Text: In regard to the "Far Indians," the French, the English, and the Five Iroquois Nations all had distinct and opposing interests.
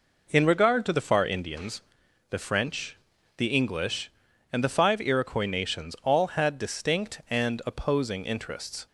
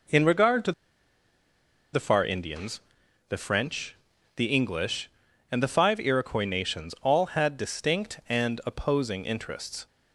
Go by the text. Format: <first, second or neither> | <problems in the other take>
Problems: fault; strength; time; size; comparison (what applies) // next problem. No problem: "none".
first | pauses between "to" and "the"; at 0.7 s; 1.2 s long